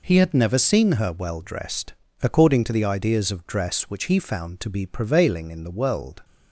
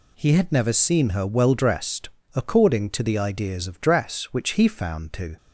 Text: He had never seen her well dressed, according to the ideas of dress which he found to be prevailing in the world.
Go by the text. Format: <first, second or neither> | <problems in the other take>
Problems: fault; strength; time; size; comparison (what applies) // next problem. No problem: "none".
first | stops before "be prevailing in the world"; at 5.3 s